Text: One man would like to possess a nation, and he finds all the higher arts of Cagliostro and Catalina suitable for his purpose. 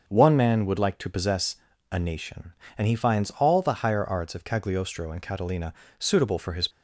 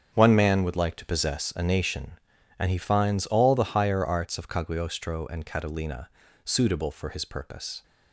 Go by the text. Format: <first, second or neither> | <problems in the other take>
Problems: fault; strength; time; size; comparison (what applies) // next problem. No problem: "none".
second | starts louder than the rest; until 1.0 s; 6.5 dB; strong in the second // pauses between "possess" and "a"; slight; at 1.5 s; 0.34 s long // pauses between "Catalina" and "suitable"; slight; at 5.7 s; 0.26 s long; slight in the second // stops before "purpose"; at 6.7 s